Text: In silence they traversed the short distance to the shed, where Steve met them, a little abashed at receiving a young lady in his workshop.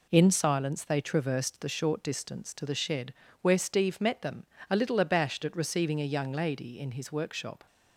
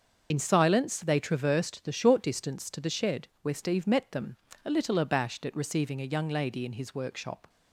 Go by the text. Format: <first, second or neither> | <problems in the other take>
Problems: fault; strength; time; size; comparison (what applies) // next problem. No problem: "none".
first | loses the start of "In"; at 0.3 s; 55 ms // starts louder than the rest; until 1.3 s; 6.5 dB